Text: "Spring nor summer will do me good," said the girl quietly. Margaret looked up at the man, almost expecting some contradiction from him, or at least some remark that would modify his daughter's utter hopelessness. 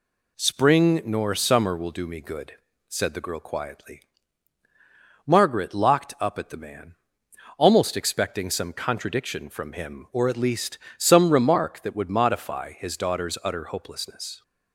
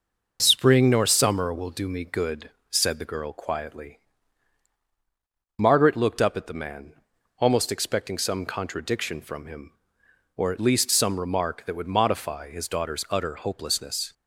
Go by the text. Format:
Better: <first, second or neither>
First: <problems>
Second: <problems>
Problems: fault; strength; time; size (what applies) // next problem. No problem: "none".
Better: second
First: says "locked" for "looked"; at 5.7 s // pauses between "least" and "some"; slight; at 10.7 s; 0.22 s long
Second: none